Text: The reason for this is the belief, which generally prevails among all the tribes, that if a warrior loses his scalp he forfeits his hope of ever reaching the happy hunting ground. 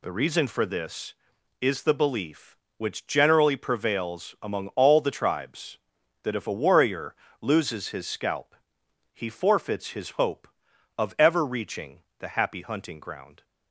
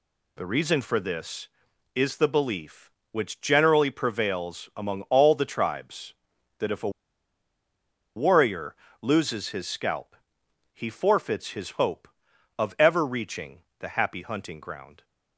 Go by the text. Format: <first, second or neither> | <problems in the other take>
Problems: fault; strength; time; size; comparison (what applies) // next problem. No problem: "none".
first | pauses between "a" and "warrior"; strong; at 6.8 s; 1.2 s long // pauses between "warrior" and "loses"; slight; at 8.7 s; 0.26 s long; slight in the first // pauses between "scalp" and "he"; noticeable; at 10.1 s; 0.58 s long; noticeable in the first // pauses between "reaching" and "the"; slight; at 13.5 s; 0.18 s long; slight in the first